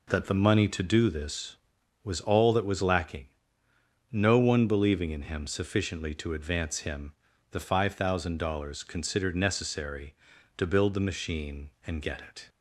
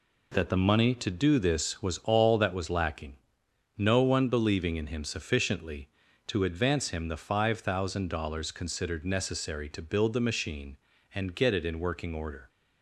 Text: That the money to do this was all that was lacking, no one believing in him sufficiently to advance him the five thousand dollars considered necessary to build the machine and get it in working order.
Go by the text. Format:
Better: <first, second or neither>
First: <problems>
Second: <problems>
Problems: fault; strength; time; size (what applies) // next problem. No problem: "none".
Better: second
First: pauses between "him" and "the"; at 7.1 s; 0.38 s long // stops before "in working order"; at 12.4 s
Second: none